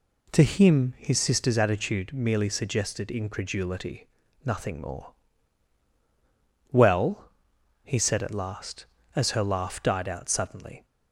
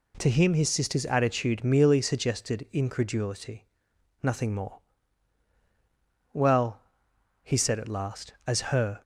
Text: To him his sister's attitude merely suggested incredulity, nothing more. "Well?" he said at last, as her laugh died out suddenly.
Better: first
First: none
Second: stops before "laugh died out suddenly"; at 9.0 s

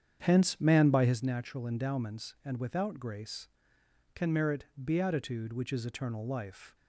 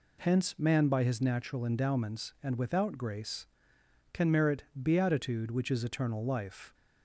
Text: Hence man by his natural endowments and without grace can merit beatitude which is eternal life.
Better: second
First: starts louder than the rest; strong; until 1.2 s; 8 dB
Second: none

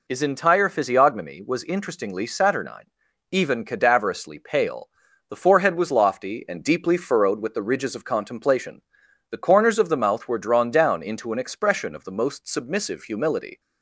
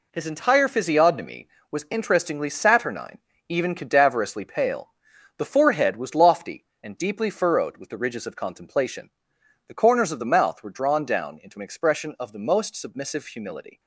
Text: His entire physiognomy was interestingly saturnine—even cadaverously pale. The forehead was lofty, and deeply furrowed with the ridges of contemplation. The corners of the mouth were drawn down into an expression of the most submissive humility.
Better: first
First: none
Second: gets quieter; strong; throughout; 8.5 dB

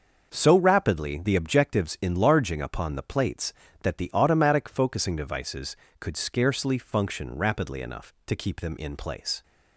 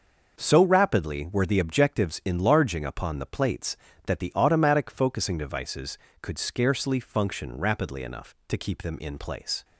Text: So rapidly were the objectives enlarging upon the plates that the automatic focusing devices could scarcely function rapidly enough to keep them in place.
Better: second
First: starts louder than the rest; noticeable; until 1.3 s; 6 dB // skips "were"; at 1.2 s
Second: starts louder than the rest; noticeable; until 1.3 s; 6 dB

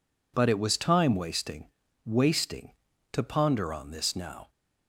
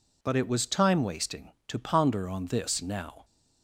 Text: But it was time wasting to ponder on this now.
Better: second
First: says "wasting" twice; at 2.0 s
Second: none

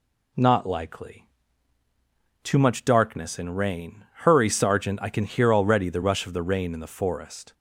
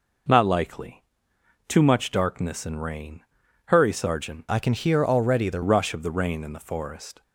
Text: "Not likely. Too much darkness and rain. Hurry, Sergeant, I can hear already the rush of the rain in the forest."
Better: first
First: none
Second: changes voice from "I" to "the"; from 4.4 to 5.6 s; 1.2 s long

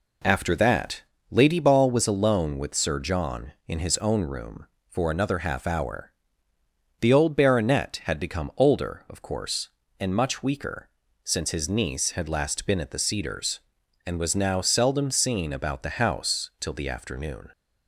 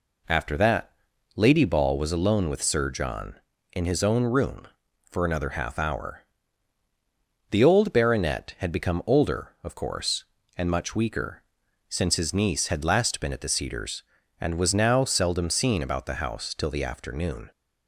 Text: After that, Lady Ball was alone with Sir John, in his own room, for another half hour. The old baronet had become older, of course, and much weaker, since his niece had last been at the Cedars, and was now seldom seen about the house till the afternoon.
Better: neither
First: none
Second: none

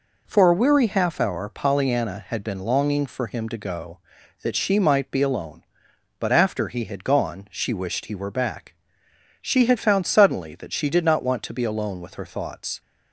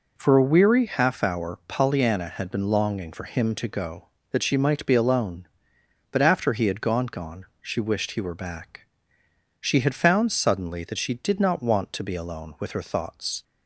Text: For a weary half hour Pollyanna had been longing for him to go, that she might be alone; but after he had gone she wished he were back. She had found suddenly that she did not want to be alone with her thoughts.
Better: first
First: none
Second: says "gone" twice; at 7.0 s

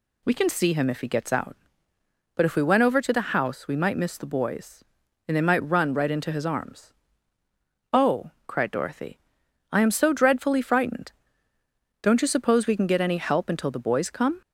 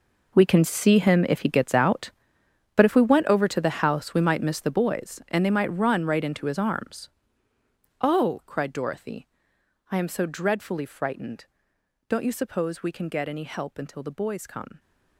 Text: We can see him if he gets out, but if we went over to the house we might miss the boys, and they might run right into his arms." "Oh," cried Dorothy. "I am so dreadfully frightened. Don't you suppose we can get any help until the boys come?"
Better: first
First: none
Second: gets quieter; strong; throughout; 14.5 dB

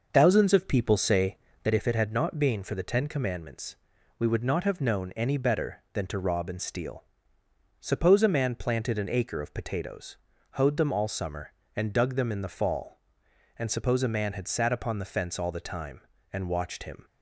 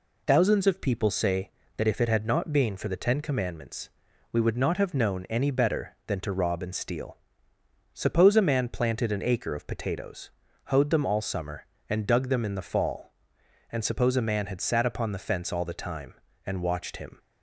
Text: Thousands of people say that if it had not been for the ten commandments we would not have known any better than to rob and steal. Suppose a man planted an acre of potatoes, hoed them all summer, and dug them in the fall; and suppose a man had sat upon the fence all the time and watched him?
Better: second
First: starts louder than the rest; noticeable; until 1.8 s; 6 dB // pauses between "commandments" and "we"; at 3.7 s; 0.42 s long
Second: pauses between "commandments" and "we"; at 3.8 s; 0.42 s long

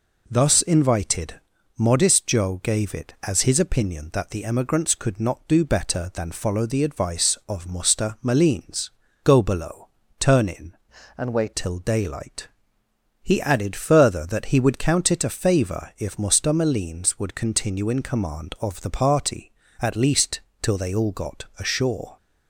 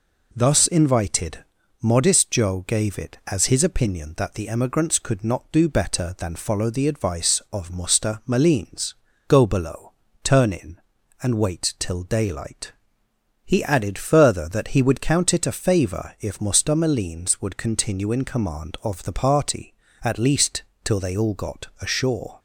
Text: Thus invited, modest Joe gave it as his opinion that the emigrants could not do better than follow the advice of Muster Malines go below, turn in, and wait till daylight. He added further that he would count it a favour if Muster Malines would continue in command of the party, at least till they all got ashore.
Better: second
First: pauses between "Malines" and "go"; slight; at 8.8 s; 0.34 s long // changes voice from "and" to "wait"; from 11.1 to 11.5 s; 0.4 s long // pauses between "least" and "till"; slight; at 20.4 s; 0.20 s long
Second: pauses between "Malines" and "go"; slight; at 8.9 s; 0.34 s long // pauses between "least" and "till"; slight; at 20.6 s; 0.20 s long

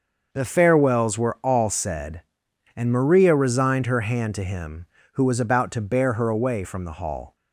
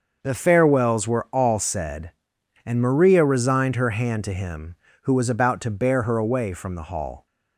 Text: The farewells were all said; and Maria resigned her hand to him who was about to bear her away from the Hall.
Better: neither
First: starts louder than the rest; noticeable; until 1.3 s; 6 dB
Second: starts louder than the rest; until 1.2 s; 6 dB

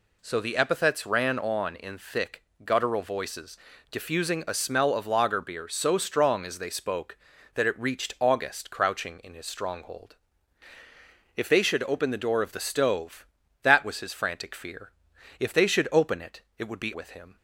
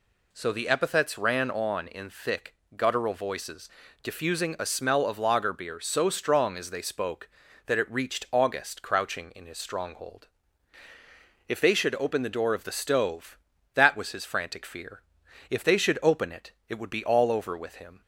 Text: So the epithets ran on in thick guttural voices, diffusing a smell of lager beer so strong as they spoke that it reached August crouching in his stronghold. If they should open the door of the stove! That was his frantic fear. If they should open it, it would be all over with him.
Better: second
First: pauses between "thick" and "guttural"; slight; at 2.4 s; 0.22 s long // skips "all over"; at 16.9 s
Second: pauses between "thick" and "guttural"; slight; at 2.5 s; 0.22 s long

